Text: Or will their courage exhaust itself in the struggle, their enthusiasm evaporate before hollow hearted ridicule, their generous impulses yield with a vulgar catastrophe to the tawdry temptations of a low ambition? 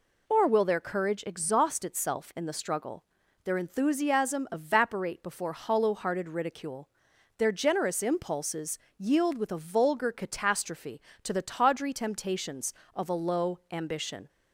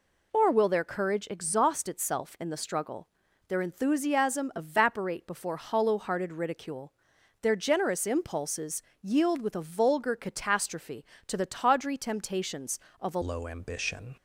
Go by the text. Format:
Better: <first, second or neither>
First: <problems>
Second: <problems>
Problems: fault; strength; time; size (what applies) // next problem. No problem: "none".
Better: first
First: pauses between "impulses" and "yield"; slight; at 8.7 s; 0.20 s long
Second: pauses between "impulses" and "yield"; slight; at 8.8 s; 0.20 s long // changes voice at "low"; from 13.2 s on; 0.9 s long